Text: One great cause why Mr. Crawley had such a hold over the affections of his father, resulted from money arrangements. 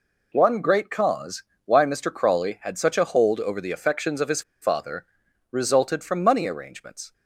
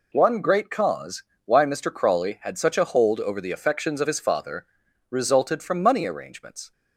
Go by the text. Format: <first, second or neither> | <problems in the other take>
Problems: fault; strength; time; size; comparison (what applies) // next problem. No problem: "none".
second | pauses between "cause" and "why"; slight; at 1.4 s; 0.22 s long; slight in the second // pauses between "his" and "father"; slight; at 4.4 s; 0.20 s long